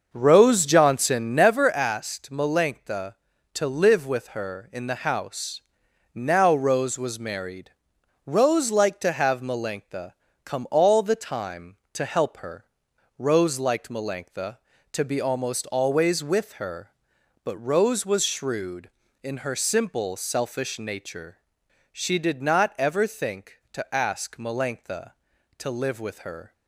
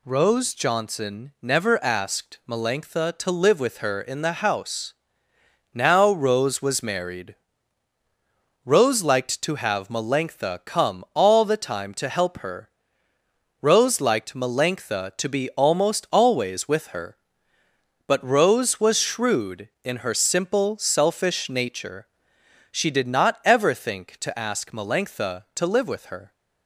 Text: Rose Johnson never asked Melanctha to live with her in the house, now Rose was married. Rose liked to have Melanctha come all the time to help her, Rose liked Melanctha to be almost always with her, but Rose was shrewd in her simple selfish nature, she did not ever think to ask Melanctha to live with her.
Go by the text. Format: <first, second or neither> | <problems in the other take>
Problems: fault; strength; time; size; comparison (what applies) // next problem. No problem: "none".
second | starts louder than the rest; until 1.6 s; 6 dB // pauses between "Melanctha" and "come"; slight; at 10.1 s; 0.32 s long